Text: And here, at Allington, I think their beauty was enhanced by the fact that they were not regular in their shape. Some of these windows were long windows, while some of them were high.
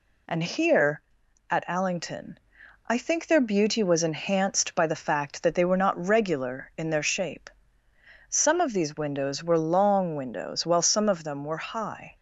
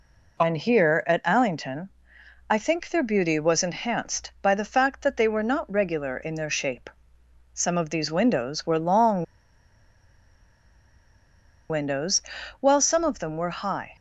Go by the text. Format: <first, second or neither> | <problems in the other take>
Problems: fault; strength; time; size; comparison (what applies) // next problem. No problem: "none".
first | pauses between "long" and "windows"; strong; at 9.2 s; 2.4 s long